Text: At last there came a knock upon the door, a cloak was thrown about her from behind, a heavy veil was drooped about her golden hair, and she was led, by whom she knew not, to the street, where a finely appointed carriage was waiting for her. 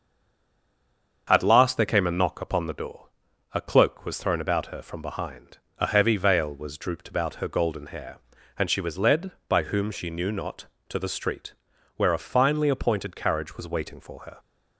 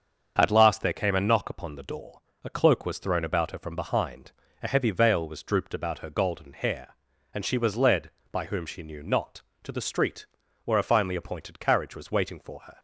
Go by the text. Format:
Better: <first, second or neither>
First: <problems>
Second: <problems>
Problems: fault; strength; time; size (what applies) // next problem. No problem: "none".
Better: second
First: stays silent before the first word; noticeable; until 1.2 s; 1.2 s long // starts louder than the rest; until 2.2 s; 7 dB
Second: starts louder than the rest; strong; until 1.3 s; 7 dB